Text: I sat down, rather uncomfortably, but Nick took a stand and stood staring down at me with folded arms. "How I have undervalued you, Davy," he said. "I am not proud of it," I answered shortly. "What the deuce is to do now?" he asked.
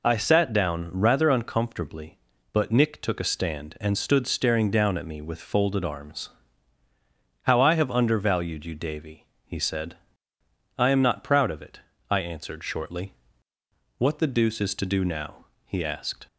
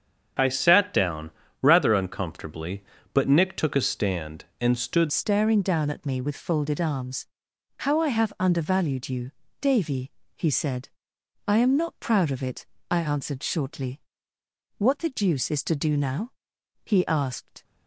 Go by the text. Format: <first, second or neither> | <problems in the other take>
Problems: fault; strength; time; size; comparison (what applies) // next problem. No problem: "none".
first | starts louder than the rest; strong; until 1.7 s; 7.5 dB // changes voice at "staring"; from 5.0 s on; 12.6 s long